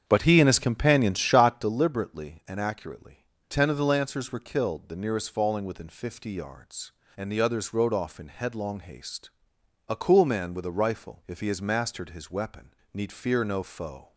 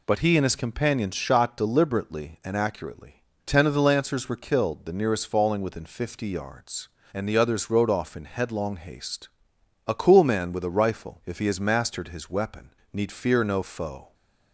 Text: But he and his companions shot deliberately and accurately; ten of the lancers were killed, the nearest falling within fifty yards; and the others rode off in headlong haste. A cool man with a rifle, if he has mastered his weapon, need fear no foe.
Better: second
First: starts louder than the rest; strong; until 1.8 s; 8 dB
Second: none

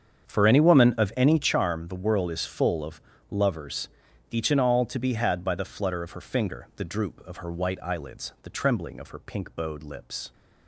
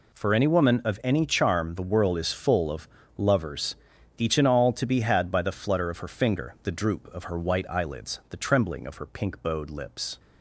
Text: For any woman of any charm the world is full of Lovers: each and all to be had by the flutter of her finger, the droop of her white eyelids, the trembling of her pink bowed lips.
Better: second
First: starts louder than the rest; strong; until 1.5 s; 7.5 dB // pauses between "of" and "Lovers"; slight; at 3.0 s; 0.30 s long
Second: pauses between "of" and "Lovers"; slight; at 2.8 s; 0.30 s long

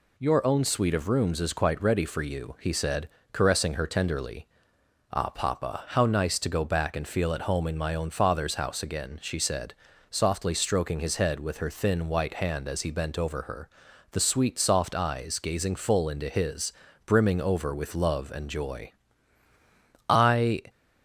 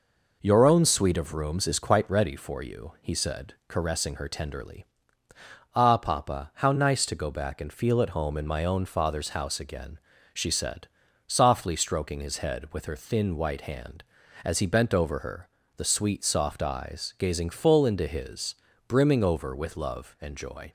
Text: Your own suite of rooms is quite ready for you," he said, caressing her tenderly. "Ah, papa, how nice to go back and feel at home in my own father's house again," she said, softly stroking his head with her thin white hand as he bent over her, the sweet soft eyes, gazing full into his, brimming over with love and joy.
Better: second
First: goes on to say "I"; from 20.0 s on; 0.54 s long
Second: none

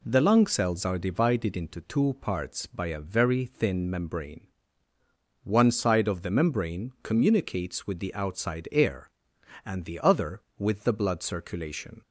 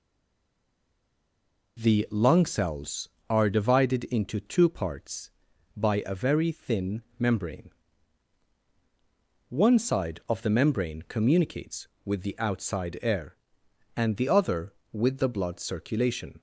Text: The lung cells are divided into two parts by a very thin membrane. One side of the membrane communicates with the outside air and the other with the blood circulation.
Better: first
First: none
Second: stays silent before the first word; noticeable; until 1.7 s; 1.7 s long // pauses between "thin" and "membrane"; slight; at 7.0 s; 0.18 s long

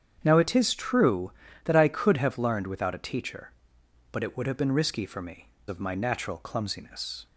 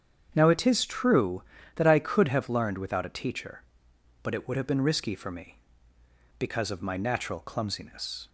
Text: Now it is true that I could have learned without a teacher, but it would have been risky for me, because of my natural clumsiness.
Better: second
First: starts louder than the rest; strong; until 1.2 s; 8 dB // skips "because"; at 5.5 s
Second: starts louder than the rest; strong; until 1.3 s; 8 dB

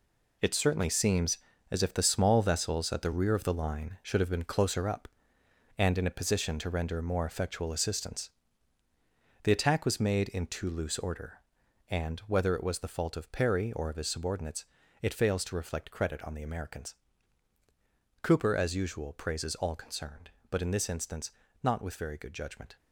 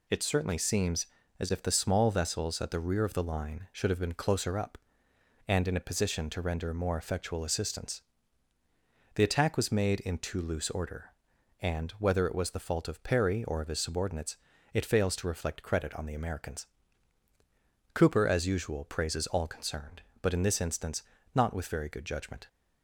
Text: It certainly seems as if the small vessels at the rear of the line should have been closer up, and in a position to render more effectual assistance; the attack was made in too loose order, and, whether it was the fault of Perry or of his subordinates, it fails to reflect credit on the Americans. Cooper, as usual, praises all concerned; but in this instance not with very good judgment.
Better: second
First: gets quieter; strong; throughout; 9 dB // pauses between "instance" and "not"; slight; at 21.2 s; 0.32 s long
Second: pauses between "instance" and "not"; slight; at 21.0 s; 0.32 s long

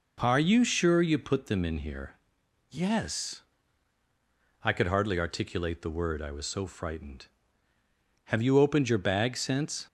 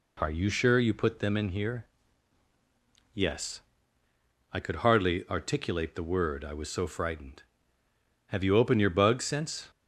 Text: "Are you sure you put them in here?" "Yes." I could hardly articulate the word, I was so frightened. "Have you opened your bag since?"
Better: first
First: none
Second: says "bug" for "bag"; at 8.9 s

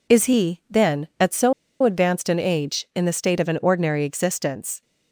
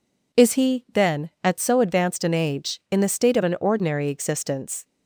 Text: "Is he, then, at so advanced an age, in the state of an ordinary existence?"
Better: second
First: pauses between "so" and "advanced"; slight; at 1.5 s; 0.30 s long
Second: none

